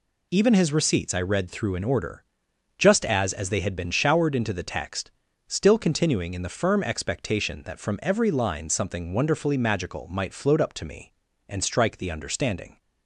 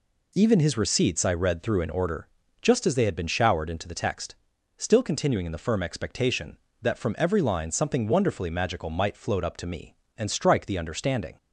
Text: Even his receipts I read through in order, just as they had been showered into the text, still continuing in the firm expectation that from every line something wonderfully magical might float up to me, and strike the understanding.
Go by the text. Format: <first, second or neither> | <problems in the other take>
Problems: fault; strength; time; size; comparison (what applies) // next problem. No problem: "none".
second | says "as" twice; at 3.3 s